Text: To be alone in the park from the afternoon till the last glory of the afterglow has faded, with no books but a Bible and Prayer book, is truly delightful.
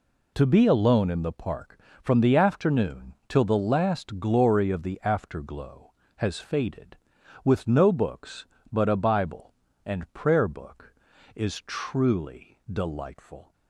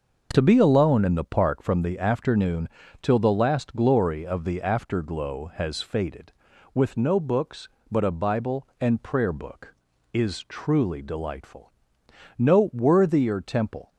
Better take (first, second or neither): first